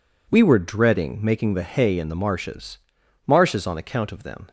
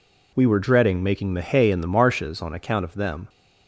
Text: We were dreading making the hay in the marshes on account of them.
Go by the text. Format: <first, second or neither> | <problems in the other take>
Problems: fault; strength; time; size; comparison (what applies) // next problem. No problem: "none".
second | says "marshes" twice; at 3.2 s